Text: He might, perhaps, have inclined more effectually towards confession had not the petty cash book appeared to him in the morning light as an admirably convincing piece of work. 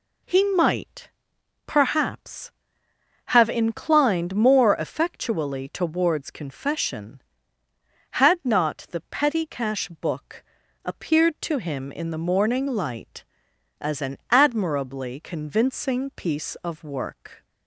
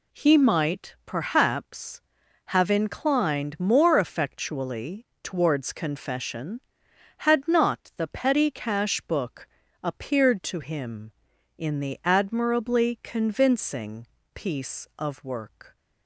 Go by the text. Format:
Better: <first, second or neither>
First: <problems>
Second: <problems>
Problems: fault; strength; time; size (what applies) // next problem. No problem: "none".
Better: first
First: pauses between "book" and "appeared"; at 10.4 s; 0.42 s long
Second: pauses between "effectually" and "towards"; slight; at 5.0 s; 0.18 s long // pauses between "book" and "appeared"; at 9.4 s; 0.38 s long // skips "morning light as an"; at 12.0 s // pauses between "convincing" and "piece"; slight; at 14.0 s; 0.28 s long